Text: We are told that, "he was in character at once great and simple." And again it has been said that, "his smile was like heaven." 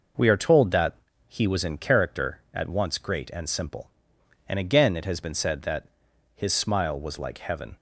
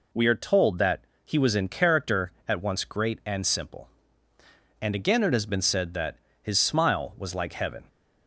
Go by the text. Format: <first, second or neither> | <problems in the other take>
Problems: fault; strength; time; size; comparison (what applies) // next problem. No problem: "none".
neither | none